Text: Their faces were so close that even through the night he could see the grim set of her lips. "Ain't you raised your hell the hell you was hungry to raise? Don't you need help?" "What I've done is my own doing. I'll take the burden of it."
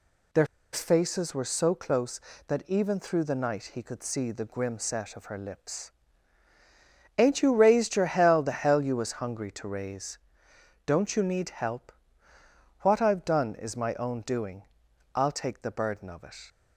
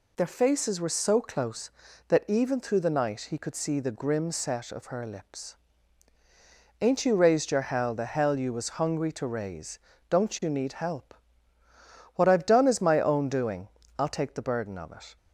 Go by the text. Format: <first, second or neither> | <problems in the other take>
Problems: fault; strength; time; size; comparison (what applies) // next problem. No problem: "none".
second | pauses between "Their" and "faces"; slight; at 0.4 s; 0.27 s long